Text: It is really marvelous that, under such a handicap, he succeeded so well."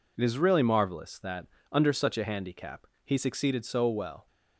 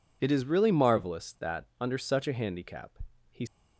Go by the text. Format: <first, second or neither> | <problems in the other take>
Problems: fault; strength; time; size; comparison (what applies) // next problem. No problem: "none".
first | stops before "succeeded so well"; at 3.4 s